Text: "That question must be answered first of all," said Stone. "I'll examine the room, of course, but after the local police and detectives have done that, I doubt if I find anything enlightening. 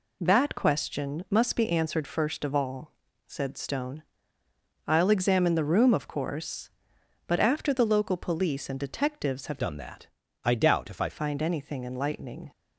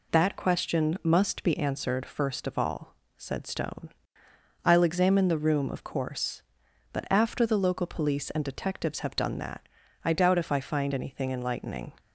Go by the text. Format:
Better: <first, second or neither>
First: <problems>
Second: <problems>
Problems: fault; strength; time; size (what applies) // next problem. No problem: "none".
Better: second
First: changes voice from "done" to "I"; from 9.5 to 11.0 s; 1.5 s long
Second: none